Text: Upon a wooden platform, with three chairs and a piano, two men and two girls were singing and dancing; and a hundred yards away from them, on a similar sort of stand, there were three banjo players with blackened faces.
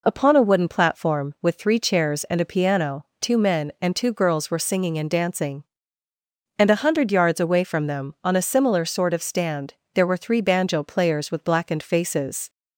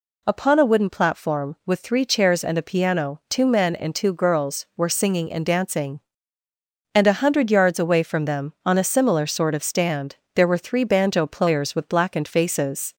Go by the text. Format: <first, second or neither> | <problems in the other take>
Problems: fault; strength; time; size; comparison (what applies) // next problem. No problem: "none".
neither | none